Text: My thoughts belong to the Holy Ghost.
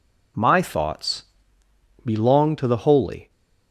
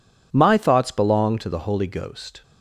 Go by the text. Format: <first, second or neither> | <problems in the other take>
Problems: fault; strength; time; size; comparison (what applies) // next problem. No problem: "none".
second | pauses between "thoughts" and "belong"; noticeable; at 1.2 s; 0.94 s long // stops before "Ghost"; at 3.2 s